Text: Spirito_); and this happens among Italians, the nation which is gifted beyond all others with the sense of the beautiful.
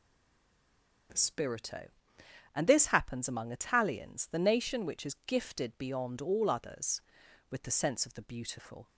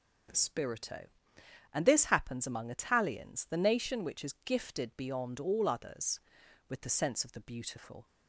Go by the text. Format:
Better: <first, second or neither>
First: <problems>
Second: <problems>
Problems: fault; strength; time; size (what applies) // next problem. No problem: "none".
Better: second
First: stays silent before the first word; until 1.0 s; 1.0 s long // starts louder than the rest; noticeable; until 2.7 s; 6 dB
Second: starts louder than the rest; noticeable; until 1.9 s; 6 dB